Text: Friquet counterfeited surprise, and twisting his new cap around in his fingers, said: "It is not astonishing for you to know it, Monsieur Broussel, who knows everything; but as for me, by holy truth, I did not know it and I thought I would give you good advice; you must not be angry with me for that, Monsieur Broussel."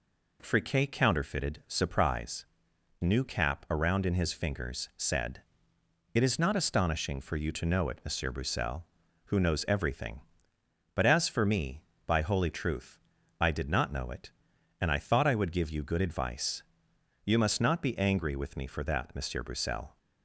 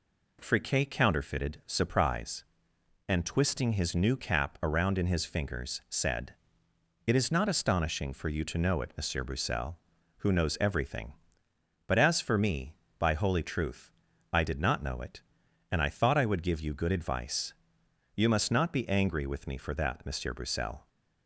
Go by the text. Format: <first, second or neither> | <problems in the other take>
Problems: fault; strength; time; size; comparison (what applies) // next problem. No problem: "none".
second | skips "and twisting his"; at 2.7 s